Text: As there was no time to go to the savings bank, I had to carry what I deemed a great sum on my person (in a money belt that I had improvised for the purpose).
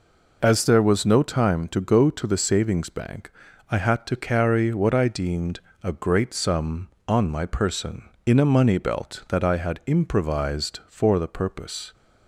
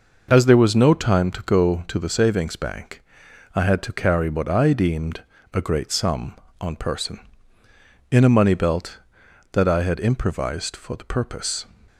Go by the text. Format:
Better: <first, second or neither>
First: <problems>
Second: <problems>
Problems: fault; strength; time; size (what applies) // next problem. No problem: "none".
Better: first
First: pauses between "deemed" and "a"; slight; at 5.5 s; 0.24 s long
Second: pauses between "deemed" and "a"; slight; at 5.2 s; 0.30 s long // skips "my"; at 6.7 s